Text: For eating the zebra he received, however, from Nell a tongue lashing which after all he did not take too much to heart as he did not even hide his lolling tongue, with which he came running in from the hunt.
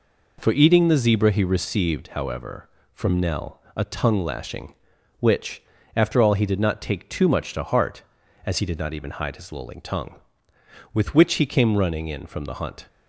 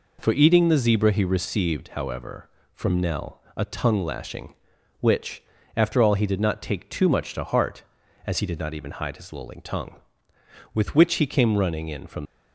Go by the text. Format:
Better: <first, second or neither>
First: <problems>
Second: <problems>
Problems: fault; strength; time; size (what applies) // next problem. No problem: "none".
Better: first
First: pauses between "Nell" and "a"; slight; at 3.5 s; 0.16 s long // pauses between "which" and "after"; slight; at 5.6 s; 0.34 s long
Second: pauses between "Nell" and "a"; slight; at 3.3 s; 0.16 s long // pauses between "which" and "after"; slight; at 5.4 s; 0.34 s long // stops before "the hunt"; at 12.2 s